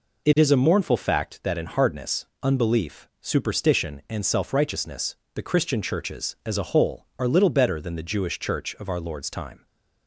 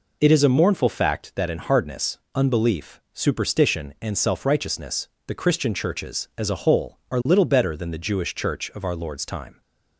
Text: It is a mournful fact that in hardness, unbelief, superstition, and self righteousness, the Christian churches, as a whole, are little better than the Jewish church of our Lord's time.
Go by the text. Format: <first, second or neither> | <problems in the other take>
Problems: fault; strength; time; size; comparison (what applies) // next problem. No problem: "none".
neither | none